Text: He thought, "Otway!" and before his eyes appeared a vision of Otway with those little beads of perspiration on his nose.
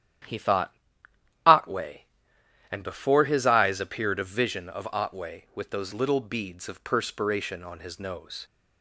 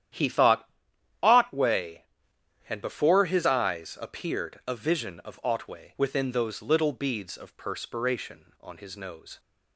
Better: first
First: starts louder than the rest; strong; until 1.9 s; 11 dB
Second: starts louder than the rest; strong; until 1.6 s; 10.5 dB // says "within" for "with"; at 5.9 s

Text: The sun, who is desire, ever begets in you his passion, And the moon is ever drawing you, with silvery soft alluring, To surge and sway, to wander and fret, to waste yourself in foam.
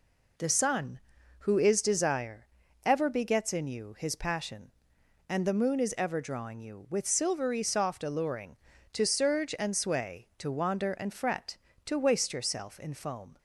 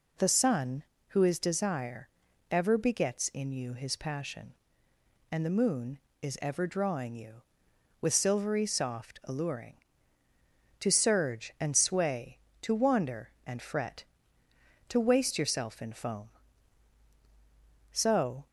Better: first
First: none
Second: goes on to say "So"; from 17.9 s on; 0.54 s long

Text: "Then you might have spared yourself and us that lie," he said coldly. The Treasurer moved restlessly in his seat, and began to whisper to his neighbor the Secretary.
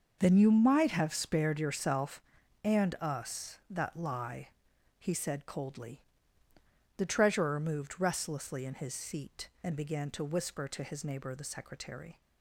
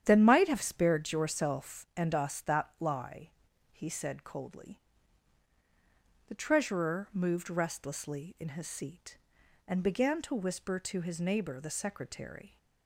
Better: first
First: starts louder than the rest; until 1.2 s; 6 dB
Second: starts louder than the rest; strong; until 1.0 s; 9.5 dB // skips "you"; at 0.2 s

